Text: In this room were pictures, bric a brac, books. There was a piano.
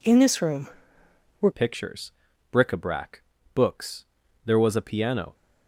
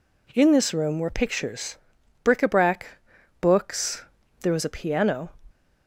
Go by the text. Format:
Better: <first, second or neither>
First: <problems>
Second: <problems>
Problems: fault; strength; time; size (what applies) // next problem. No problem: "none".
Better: second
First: changes voice at "pictures"; from 1.5 s on; 3.8 s long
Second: none